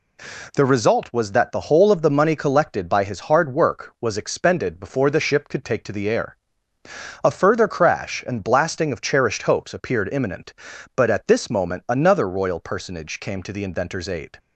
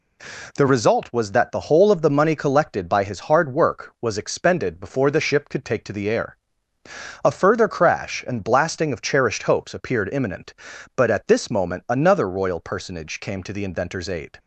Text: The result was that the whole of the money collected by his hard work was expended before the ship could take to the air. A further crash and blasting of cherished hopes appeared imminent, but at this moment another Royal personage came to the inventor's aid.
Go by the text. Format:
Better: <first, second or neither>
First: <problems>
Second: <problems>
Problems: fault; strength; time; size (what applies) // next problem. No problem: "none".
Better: neither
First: none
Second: none